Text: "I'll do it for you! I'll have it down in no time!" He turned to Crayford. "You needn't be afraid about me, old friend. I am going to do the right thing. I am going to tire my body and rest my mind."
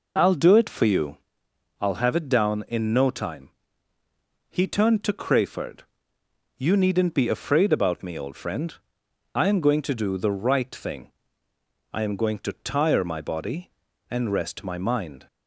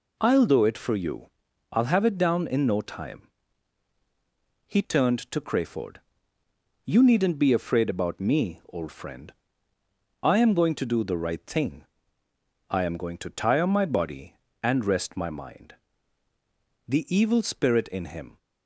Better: first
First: none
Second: goes on to say "The evil spirit in him"; from 16.8 s on; 1.5 s long

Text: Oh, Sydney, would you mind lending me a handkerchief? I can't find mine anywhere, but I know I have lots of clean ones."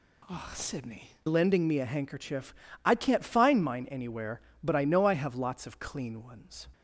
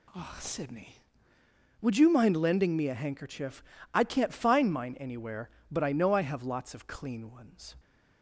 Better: second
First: skips "would you mind"; at 1.1 s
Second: none

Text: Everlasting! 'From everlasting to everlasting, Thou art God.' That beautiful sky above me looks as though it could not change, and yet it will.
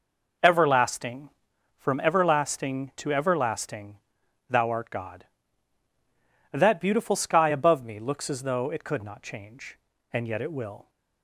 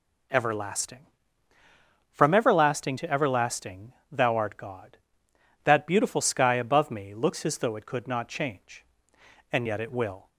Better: neither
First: none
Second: none

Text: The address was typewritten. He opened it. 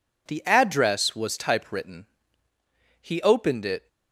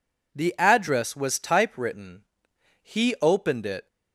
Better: neither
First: none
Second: none

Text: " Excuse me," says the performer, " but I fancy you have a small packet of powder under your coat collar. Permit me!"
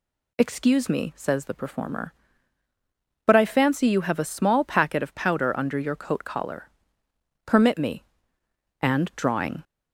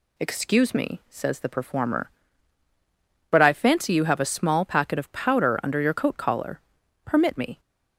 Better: second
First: goes on to say "and drawing"; noticeable; from 8.8 s on; 0.82 s long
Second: none

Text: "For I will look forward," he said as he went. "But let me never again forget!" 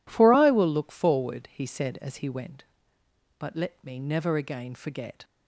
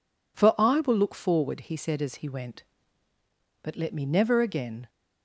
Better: first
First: none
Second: stops before "forget"; at 4.8 s

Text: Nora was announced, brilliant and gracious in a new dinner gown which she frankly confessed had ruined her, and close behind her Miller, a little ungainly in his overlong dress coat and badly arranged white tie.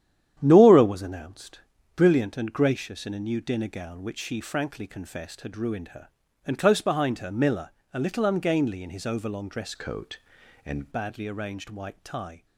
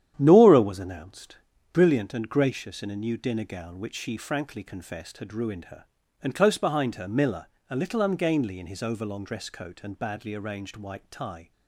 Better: second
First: starts louder than the rest; strong; until 1.3 s; 10 dB // changes voice from "coat" to "and"; from 9.7 to 10.9 s; 1.2 s long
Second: starts louder than the rest; strong; until 1.1 s; 10 dB

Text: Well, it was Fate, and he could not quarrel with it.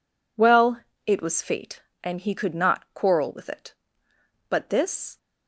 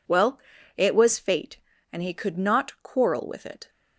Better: second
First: goes on to say "But this"; noticeable; from 4.4 s on; 0.68 s long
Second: none

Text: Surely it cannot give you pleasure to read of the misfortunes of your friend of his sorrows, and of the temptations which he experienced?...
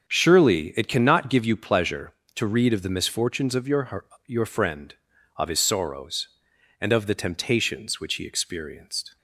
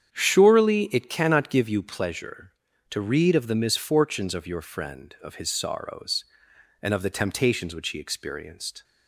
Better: second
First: starts louder than the rest; strong; until 1.1 s; 7 dB // says "your" twice; at 4.2 s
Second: starts louder than the rest; strong; until 1.2 s; 8.5 dB

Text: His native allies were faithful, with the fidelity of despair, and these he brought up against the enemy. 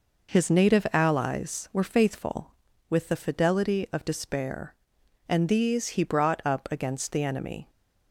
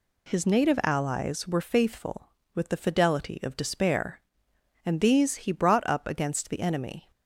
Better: neither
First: none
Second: none

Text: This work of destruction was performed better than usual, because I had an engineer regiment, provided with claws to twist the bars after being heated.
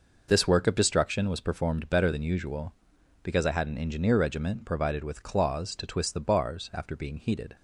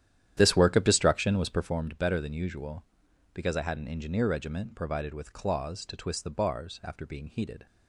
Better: first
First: none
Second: starts louder than the rest; strong; until 1.8 s; 11 dB

